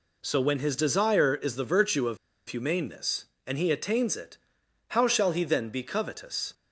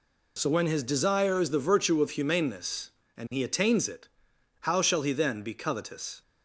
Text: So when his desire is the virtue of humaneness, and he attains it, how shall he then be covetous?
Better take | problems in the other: second | pauses between "of" and "humaneness"; slight; at 2.1 s; 0.31 s long

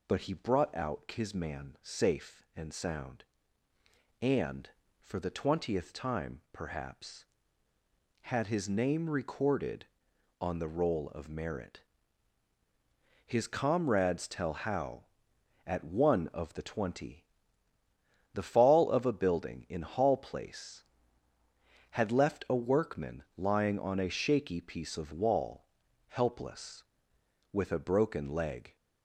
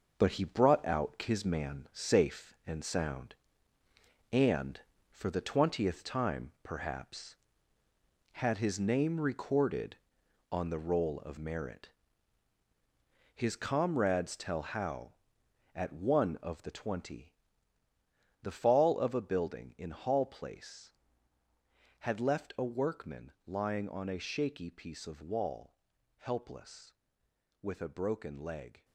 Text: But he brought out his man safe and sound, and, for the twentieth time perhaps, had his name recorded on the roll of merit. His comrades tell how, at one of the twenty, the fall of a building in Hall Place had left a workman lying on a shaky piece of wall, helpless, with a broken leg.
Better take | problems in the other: first | gets quieter; strong; throughout; 7.5 dB // pauses between "workman" and "lying"; slight; at 23.3 s; 0.16 s long; slight in the first

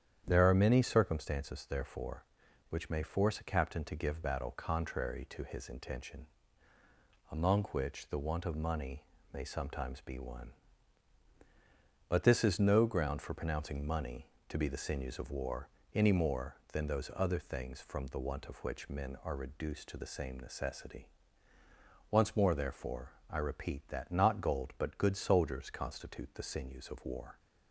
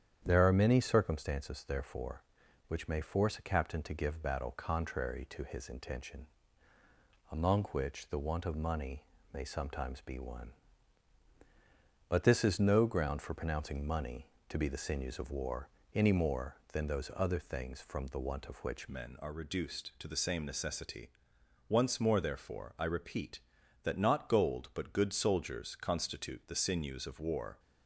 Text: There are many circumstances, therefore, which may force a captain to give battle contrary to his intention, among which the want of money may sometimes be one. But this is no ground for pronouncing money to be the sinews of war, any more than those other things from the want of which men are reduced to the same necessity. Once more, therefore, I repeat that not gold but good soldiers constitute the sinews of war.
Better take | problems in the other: first | starts louder than the rest; strong; until 1.2 s; 9 dB; strong in the first // pauses between "money" and "may"; slight; at 9.0 s; 0.30 s long; slight in the first // changes voice at "men"; from 18.8 s on; 8.7 s long

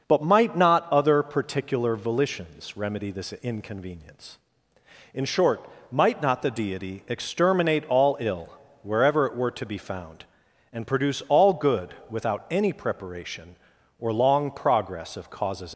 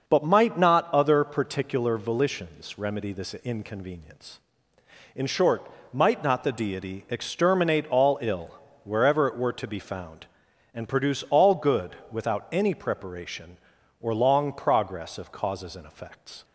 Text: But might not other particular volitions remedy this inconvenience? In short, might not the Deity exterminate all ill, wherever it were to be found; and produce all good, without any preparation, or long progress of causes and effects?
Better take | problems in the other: second | starts louder than the rest; noticeable; until 1.1 s; 6 dB; noticeable in the second // stops before "and effects"; at 15.7 s

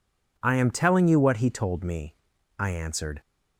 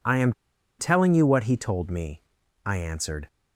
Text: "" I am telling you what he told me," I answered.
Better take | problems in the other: first | pauses between "am" and "telling"; noticeable; at 0.3 s; 0.46 s long

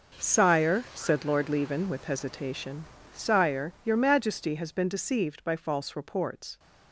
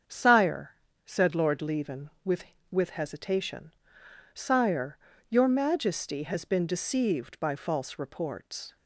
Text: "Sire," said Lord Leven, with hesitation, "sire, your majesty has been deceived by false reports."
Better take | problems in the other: first | starts louder than the rest; strong; until 1.4 s; 7.5 dB // says "with" twice; at 2.6 s

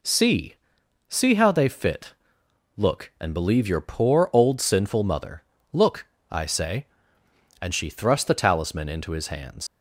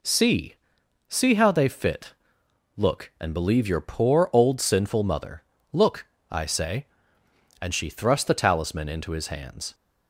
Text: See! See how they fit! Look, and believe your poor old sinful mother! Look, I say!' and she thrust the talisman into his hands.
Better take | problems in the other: second | leaves "hands" unfinished; at 9.6 s; 75 ms

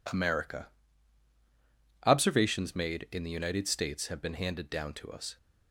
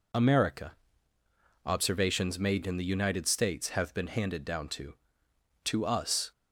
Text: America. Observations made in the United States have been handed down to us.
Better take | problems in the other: first | says "to" twice; at 5.6 s

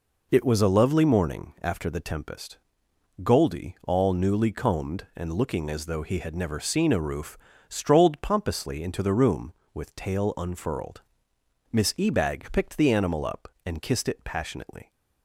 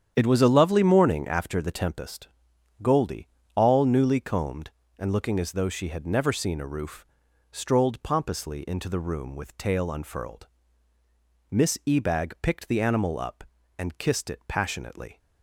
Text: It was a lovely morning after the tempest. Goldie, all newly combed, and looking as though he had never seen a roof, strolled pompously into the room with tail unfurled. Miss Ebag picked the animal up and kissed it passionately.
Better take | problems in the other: first | starts louder than the rest; strong; until 1.1 s; 9 dB // says "she" for "he"; at 5.6 s

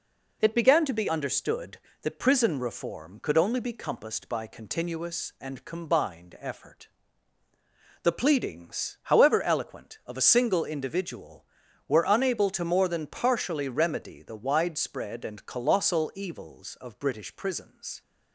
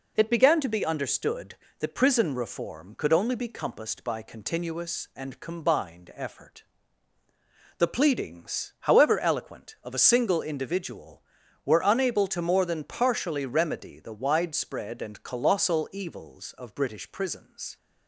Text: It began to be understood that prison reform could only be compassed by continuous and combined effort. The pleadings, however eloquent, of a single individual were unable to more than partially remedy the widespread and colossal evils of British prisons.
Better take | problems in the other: neither | none

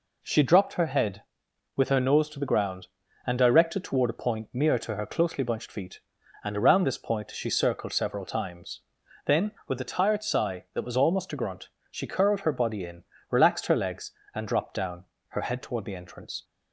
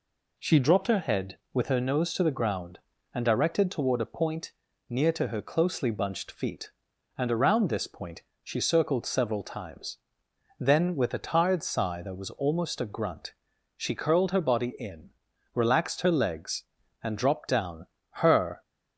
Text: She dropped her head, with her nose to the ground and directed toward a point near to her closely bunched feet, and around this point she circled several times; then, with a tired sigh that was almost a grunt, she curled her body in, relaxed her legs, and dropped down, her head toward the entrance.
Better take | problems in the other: first | pauses between "point" and "near"; at 4.5 s; 0.38 s long // pauses between "point" and "she"; slight; at 8.2 s; 0.22 s long // stops before "head toward the entrance"; at 18.6 s

